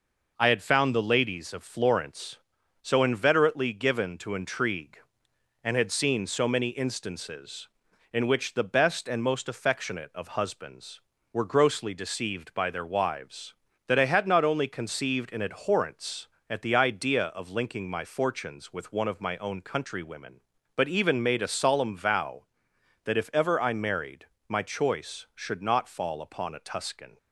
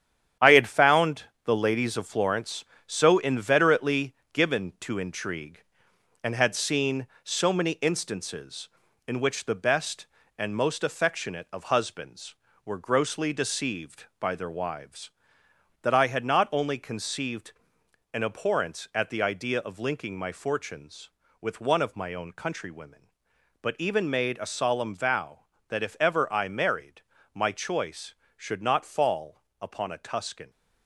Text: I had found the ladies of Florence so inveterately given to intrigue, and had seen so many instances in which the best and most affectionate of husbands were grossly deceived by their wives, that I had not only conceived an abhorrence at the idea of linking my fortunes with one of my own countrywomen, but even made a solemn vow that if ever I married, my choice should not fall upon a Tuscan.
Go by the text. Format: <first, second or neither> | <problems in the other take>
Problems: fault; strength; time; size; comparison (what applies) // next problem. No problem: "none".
first | gets quieter; strong; throughout; 8.5 dB // pauses between "found" and "the"; slight; at 1.2 s; 0.22 s long // pauses between "inveterately" and "given"; slight; at 4.1 s; 0.18 s long // pauses between "conceived" and "an"; noticeable; at 17.5 s; 0.62 s long // pauses between "fall" and "upon"; slight; at 29.4 s; 0.18 s long